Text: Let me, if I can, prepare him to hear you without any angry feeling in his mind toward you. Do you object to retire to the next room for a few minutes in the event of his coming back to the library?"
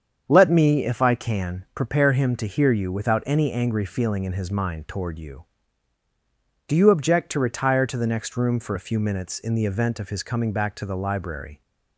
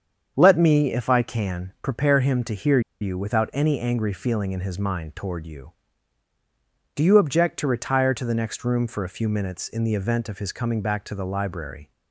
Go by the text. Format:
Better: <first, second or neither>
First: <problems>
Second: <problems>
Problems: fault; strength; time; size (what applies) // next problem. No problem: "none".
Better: first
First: starts louder than the rest; strong; until 1.2 s; 7.5 dB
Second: starts louder than the rest; strong; until 1.3 s; 7.5 dB // pauses between "hear" and "you"; slight; at 2.8 s; 0.21 s long